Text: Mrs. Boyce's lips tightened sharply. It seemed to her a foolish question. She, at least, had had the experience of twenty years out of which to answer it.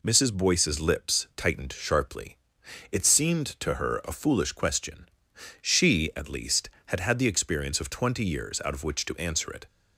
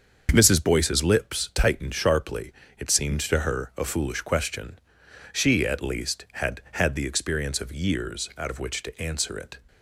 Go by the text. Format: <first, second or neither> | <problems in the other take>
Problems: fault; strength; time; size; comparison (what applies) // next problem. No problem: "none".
first | starts louder than the rest; until 1.3 s; 6.5 dB // skips "twenty"; at 7.7 s